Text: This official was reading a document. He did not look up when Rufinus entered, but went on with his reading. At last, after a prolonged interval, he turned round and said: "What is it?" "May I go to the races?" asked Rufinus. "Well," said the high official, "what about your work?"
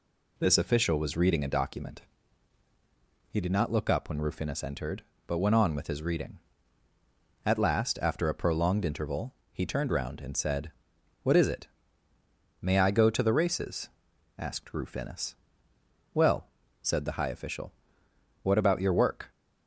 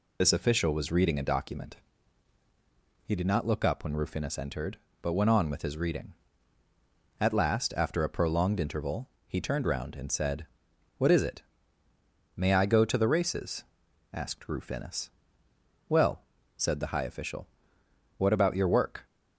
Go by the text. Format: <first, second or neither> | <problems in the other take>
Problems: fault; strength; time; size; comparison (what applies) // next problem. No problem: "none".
first | loses the start of "This"; at 0.2 s; 70 ms